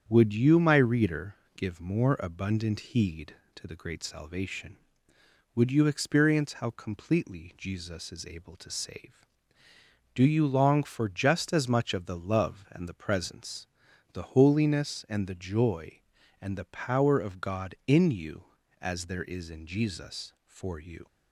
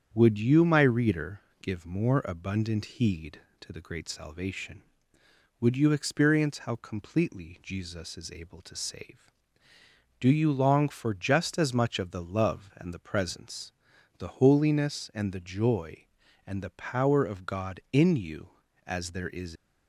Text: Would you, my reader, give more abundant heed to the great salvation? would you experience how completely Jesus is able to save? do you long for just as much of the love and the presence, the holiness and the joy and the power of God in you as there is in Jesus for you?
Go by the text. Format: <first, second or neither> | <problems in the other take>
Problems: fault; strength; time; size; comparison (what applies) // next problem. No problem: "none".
first | starts louder than the rest; strong; until 1.1 s; 8 dB; strong in the first // stops before "in Jesus for you"; at 19.5 s